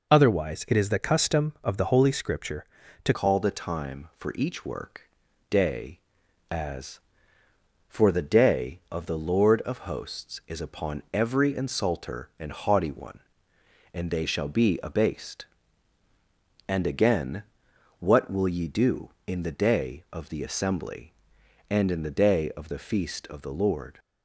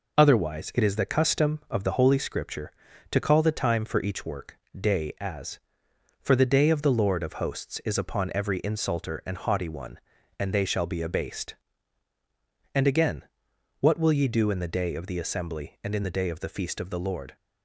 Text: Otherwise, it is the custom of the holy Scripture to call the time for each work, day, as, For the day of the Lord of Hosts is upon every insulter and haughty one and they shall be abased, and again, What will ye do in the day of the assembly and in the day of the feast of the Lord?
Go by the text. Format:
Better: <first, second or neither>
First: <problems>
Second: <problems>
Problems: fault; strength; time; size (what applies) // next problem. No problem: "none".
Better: second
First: changes voice at "call"; from 3.1 s on; 20.8 s long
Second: none